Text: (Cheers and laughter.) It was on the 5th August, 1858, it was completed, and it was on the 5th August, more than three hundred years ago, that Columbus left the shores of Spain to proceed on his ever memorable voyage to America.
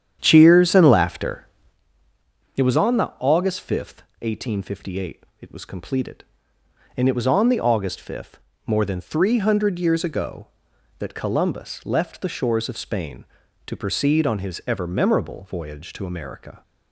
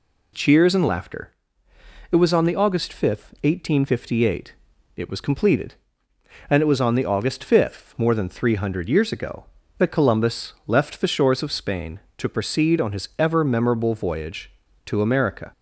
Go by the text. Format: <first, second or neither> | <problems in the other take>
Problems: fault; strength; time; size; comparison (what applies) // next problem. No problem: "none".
second | starts louder than the rest; strong; until 2.0 s; 9.5 dB